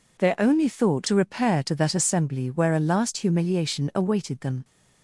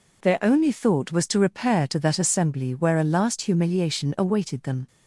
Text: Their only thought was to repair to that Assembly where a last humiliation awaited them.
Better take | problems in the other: second | skips "was"; at 1.0 s

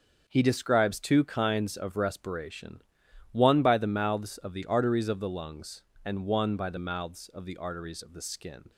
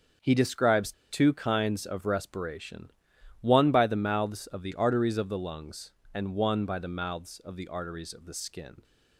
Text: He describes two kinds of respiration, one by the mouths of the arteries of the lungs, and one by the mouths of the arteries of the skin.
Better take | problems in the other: first | starts louder than the rest; until 1.4 s; 7 dB; also in the first // pauses between "describes" and "two"; slight; at 0.9 s; 0.19 s long

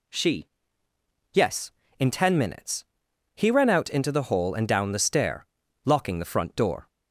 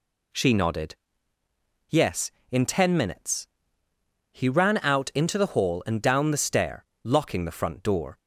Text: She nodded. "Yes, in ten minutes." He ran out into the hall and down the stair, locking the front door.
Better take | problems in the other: second | skips "nodded"; at 0.9 s

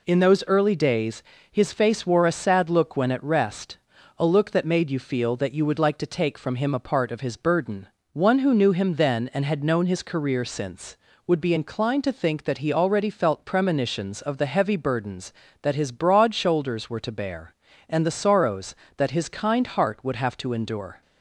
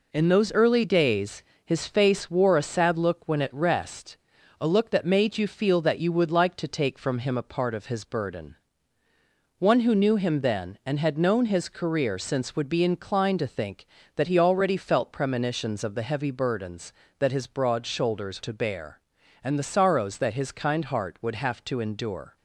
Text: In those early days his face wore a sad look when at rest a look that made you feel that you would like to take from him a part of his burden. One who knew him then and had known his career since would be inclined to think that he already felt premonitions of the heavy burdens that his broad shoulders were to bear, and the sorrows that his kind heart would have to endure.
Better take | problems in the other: first | pauses between "days" and "his"; slight; at 1.4 s; 0.24 s long; slight in the first // pauses between "rest" and "a"; at 4.1 s; 0.42 s long; also in the first // skips "were"; at 18.4 s

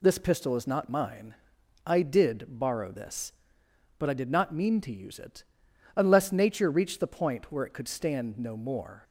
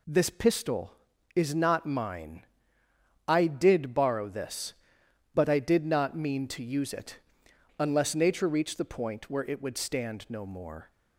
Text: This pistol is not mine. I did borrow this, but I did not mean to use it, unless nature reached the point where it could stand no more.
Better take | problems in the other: first | says "would" for "could"; at 9.6 s

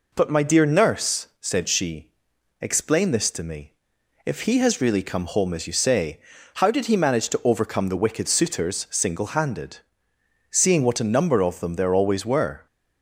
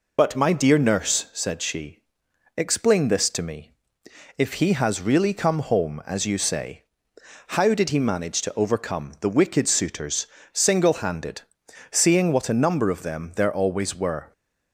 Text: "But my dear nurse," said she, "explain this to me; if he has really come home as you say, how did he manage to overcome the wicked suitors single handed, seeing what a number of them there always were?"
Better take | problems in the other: first | loses the start of "But"; at 0.1 s; 35 ms // pauses between "suitors" and "single"; slight; at 10.2 s; 0.28 s long

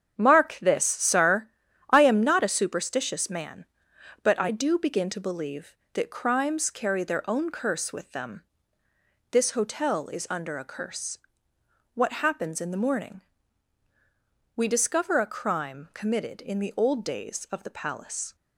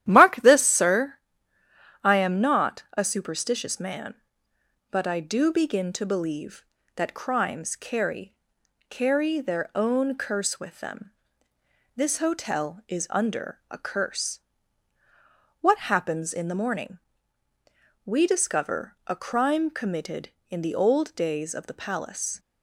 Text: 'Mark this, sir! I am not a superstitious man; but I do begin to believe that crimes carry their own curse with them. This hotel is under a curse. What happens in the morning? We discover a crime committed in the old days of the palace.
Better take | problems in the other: first | starts louder than the rest; strong; until 1.0 s; 12 dB; strong in the first // says "carry" twice; at 8.8 s

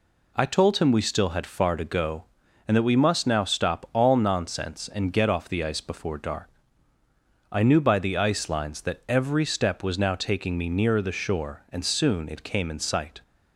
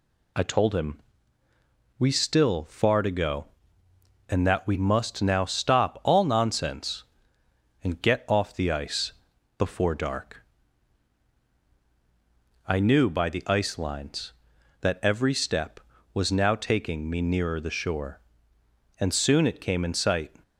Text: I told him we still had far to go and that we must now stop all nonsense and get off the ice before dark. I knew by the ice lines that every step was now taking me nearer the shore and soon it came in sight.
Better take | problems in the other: first | pauses between "him" and "we"; noticeable; at 0.9 s; 0.98 s long // skips "had"; at 2.6 s // pauses between "ice" and "before"; noticeable; at 9.1 s; 0.46 s long

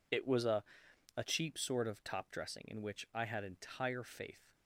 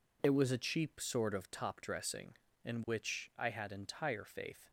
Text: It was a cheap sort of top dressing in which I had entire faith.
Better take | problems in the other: second | says "a" twice; at 1.1 s

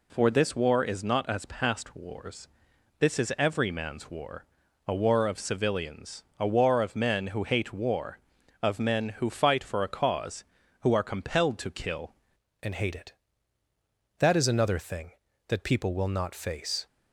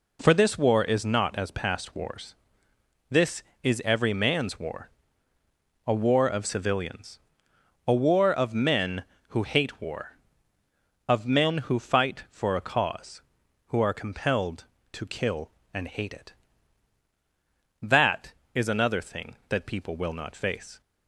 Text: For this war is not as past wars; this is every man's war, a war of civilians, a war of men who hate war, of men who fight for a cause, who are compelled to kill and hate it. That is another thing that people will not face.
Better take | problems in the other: second | changes voice at "and"; from 12.6 s on; 4.2 s long

